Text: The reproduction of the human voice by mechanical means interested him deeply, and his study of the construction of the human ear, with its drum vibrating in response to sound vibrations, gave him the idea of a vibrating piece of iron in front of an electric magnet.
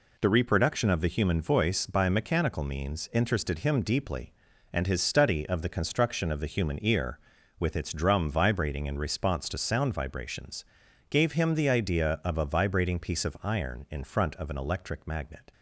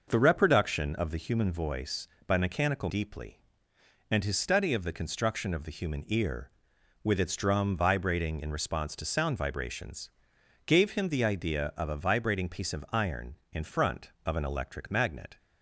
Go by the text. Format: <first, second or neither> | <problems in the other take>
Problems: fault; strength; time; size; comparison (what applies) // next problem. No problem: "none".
first | skips "means interested him"; at 2.8 s